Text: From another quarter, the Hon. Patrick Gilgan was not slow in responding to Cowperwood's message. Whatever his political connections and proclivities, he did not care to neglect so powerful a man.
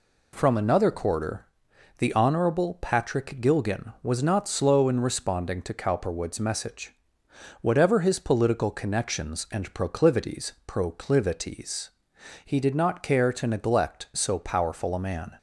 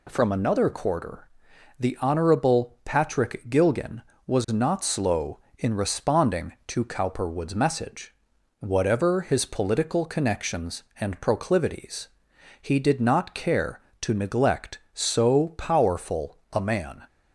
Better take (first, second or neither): second